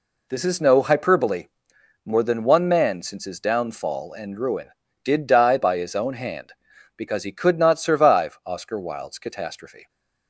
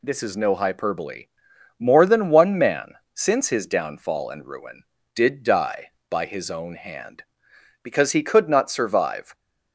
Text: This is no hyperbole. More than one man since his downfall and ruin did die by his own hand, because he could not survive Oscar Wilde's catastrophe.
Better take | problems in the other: first | pauses between "man" and "since"; slight; at 2.9 s; 0.18 s long // stops before "Oscar Wilde's catastrophe"; at 9.3 s

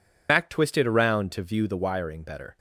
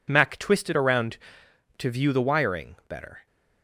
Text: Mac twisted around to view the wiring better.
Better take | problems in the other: second | loses the start of "Mac"; at 0.2 s; 75 ms

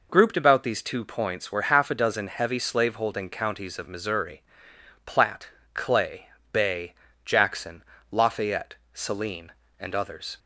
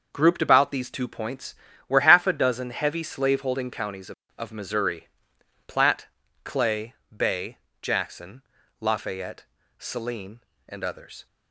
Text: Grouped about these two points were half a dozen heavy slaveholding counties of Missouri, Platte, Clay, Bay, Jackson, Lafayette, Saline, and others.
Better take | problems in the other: first | starts louder than the rest; noticeable; until 1.1 s; 6 dB // says "of" twice; at 4.3 s

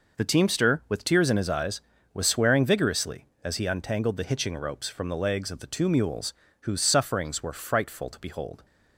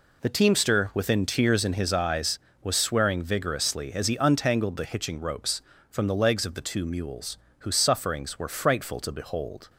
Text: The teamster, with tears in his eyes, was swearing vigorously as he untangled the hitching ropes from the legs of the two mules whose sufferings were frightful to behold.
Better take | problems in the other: first | says "within" for "with"; at 0.9 s // pauses between "mules" and "whose"; slight; at 7.3 s; 0.22 s long; slight in the first

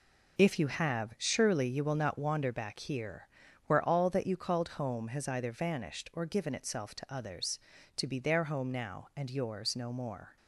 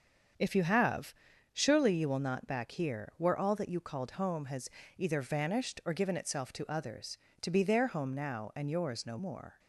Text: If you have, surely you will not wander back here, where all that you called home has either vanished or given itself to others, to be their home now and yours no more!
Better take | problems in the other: first | starts louder than the rest; until 1.7 s; 7 dB // skips "wander"; at 2.4 s // pauses between "has" and "either"; slight; at 4.6 s; 0.28 s long

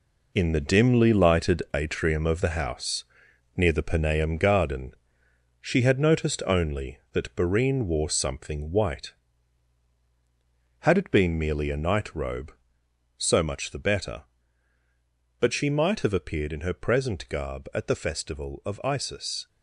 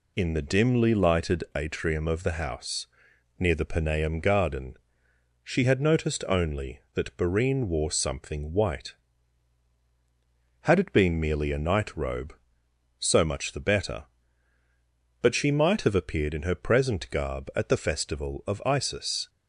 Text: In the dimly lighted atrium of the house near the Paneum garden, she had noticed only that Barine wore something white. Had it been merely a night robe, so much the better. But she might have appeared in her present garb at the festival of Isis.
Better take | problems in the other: second | gets quieter; strong; throughout; 8 dB // pauses between "house" and "near"; noticeable; at 3.0 s; 0.50 s long; noticeable in the second

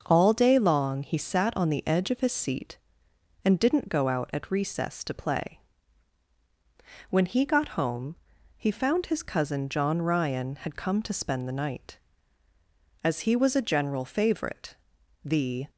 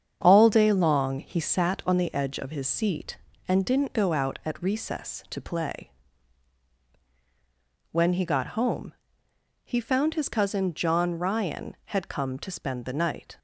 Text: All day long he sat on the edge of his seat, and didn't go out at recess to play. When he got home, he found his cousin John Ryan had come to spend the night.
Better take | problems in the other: second | starts louder than the rest; until 1.0 s; 6.5 dB; strong in the second // goes on to say "As he was a general favorite the"; strong; from 13.0 s on; 2.6 s long

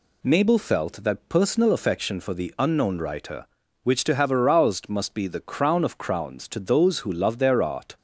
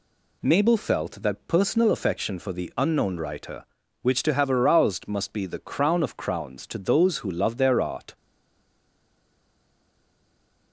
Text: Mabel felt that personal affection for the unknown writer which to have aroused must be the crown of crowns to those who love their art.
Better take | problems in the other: first | stays silent after the last word; strong; from 8.1 s on; 2.6 s long

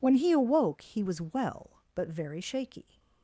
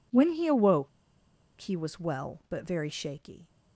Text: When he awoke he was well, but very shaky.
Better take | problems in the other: first | pauses between "awoke" and "he"; noticeable; at 0.8 s; 0.69 s long

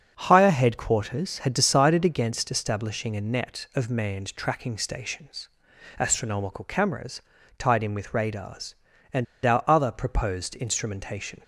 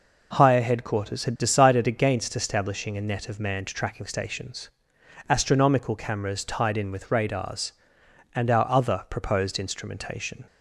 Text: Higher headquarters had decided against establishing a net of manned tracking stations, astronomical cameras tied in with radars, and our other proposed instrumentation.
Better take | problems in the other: second | starts louder than the rest; until 1.1 s; 6.5 dB // pauses between "cameras" and "tied"; at 7.2 s; 0.38 s long // pauses between "and" and "our"; slight; at 9.2 s; 0.19 s long

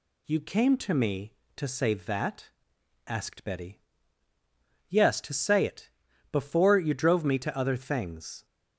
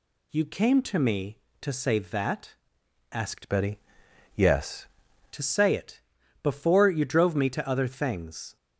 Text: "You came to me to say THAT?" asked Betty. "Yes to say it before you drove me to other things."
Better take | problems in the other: first | changes voice from "Betty" to "Yes"; from 3.4 to 4.8 s; 1.4 s long // pauses between "it" and "before"; at 5.9 s; 0.42 s long; also in the first

